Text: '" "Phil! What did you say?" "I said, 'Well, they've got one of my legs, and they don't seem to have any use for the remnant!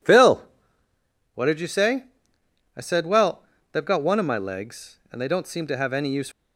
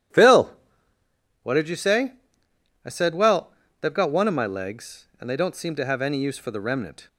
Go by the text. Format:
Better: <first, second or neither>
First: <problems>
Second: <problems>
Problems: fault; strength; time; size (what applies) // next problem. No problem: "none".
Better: second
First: stops before "for the remnant"; at 6.3 s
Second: none